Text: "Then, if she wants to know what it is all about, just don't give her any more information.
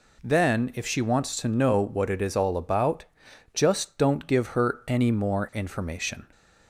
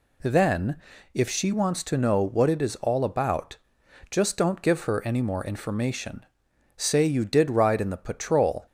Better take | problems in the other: first | goes on to say "Say you did ride in the patrol"; strong; from 6.7 s on; 1.9 s long

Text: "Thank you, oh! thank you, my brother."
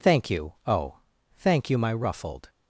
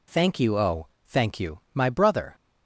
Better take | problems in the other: second | says "ruffled" for "brother"; at 1.9 s

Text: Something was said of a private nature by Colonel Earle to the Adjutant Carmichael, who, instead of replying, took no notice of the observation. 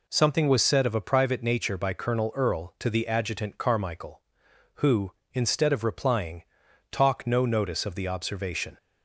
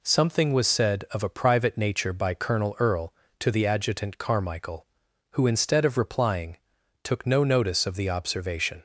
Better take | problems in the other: second | says "talk" for "took"; at 6.9 s

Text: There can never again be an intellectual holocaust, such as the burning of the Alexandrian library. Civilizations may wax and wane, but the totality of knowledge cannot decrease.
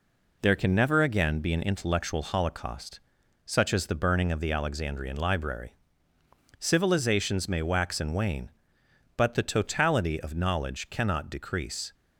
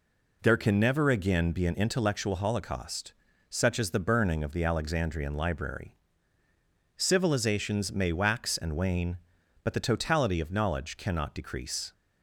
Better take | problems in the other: neither | none

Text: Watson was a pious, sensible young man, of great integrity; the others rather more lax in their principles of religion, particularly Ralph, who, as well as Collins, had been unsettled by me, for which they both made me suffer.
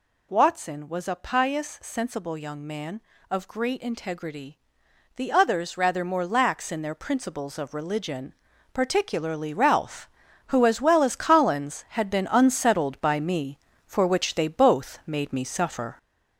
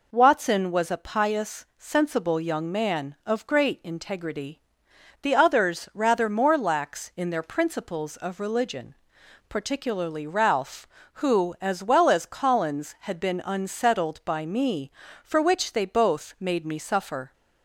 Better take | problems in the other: second | gets louder; noticeable; throughout; 4.5 dB

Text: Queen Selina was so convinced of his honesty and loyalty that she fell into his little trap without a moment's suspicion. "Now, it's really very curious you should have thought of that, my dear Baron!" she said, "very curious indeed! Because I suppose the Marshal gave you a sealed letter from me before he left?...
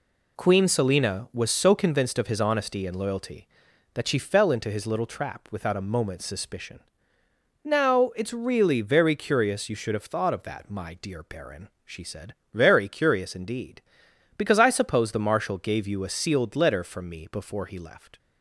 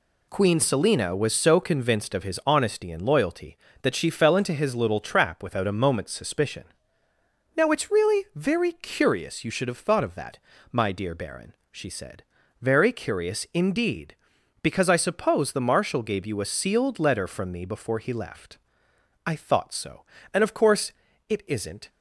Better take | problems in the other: first | goes on to say "I thought so and of course it isn't"; strong; from 19.2 s on; 2.6 s long

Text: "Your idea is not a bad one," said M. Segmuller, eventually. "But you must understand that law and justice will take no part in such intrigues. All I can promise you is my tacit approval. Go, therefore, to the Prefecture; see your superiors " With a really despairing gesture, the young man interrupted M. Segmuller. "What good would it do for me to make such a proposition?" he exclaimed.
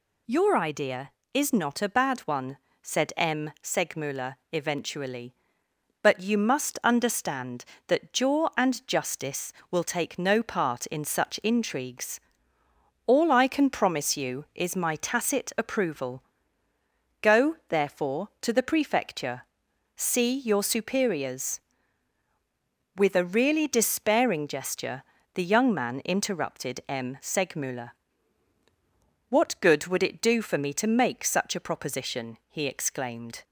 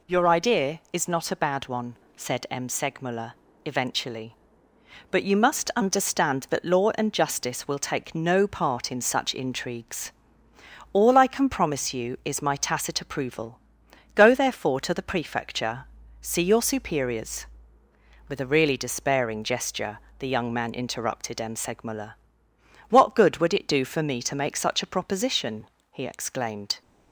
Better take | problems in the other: second | says "jaw" for "law"; at 8.1 s

